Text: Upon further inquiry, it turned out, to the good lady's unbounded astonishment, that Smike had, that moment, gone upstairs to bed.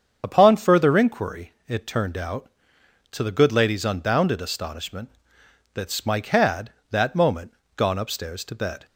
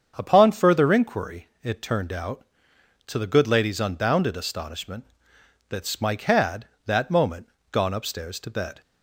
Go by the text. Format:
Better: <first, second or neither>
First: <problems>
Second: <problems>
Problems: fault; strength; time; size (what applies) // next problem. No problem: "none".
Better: second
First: loses the start of "Upon"; at 0.2 s; 55 ms // starts louder than the rest; strong; until 1.2 s; 7 dB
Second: starts louder than the rest; strong; until 1.1 s; 7 dB